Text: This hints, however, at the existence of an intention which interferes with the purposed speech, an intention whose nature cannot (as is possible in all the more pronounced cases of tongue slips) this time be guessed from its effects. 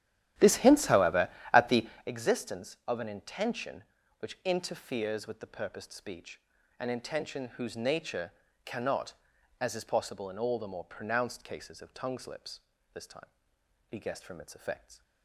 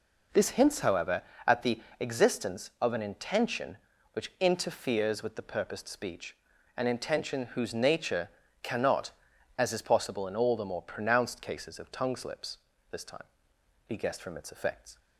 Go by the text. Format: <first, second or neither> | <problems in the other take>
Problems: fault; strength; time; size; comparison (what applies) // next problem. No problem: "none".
second | starts louder than the rest; strong; until 2.1 s; 12 dB // pauses between "the" and "existence"; slight; at 1.8 s; 0.18 s long; slight in the second // pauses between "nature" and "cannot"; slight; at 8.3 s; 0.32 s long; slight in the second // pauses between "time" and "be"; noticeable; at 13.2 s; 0.62 s long; noticeable in the second